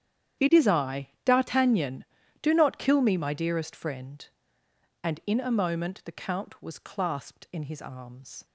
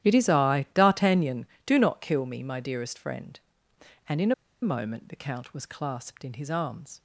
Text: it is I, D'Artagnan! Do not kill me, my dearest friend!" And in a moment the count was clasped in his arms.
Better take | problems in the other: first | starts louder than the rest; strong; until 1.1 s; 12 dB; strong in the first // pauses between "in" and "a"; slight; at 4.3 s; 0.29 s long

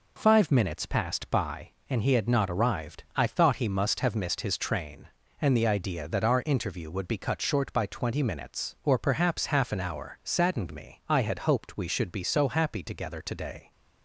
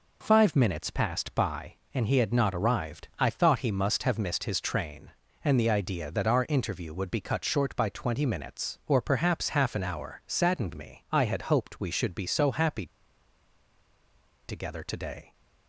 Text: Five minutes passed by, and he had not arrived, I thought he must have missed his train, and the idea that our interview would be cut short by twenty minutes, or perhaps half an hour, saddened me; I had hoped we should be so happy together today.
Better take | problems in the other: first | pauses between "happy" and "together"; strong; at 12.8 s; 1.6 s long

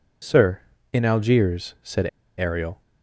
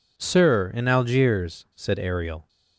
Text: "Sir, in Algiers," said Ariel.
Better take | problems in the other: second | pauses between "said" and "Ariel"; slight; at 2.0 s; 0.30 s long

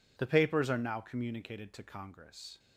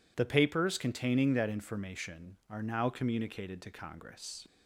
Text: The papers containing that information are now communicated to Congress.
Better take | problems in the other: second | skips "containing that information"; at 0.7 s

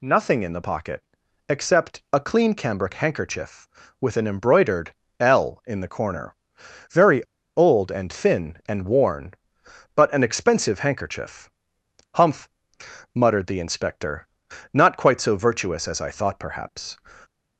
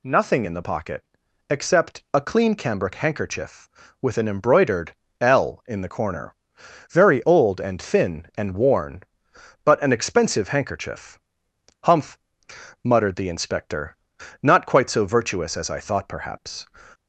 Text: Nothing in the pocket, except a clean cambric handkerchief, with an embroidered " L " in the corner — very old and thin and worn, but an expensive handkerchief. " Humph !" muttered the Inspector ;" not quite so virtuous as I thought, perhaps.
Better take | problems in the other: second | pauses between "very" and "old"; slight; at 7.2 s; 0.33 s long

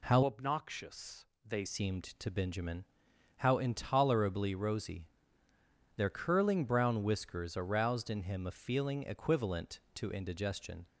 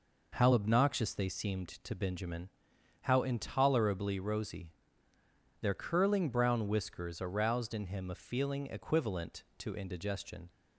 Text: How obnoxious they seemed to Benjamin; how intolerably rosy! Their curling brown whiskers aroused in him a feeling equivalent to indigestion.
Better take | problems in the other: second | changes voice from "obnoxious" to "they"; from 0.2 to 1.6 s; 1.4 s long // pauses between "obnoxious" and "they"; slight; at 1.2 s; 0.18 s long

